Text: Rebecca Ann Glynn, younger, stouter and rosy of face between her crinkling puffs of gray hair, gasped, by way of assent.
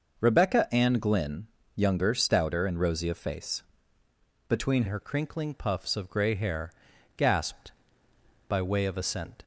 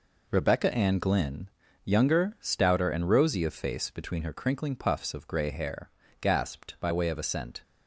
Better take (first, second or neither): second